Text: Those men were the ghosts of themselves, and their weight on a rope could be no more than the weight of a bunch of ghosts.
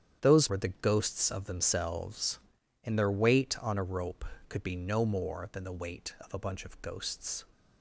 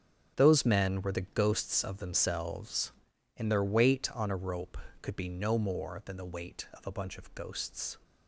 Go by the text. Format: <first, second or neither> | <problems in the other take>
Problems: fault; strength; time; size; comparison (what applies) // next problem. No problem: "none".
second | starts louder than the rest; strong; until 1.2 s; 9 dB; strong in the second // skips "men"; at 0.4 s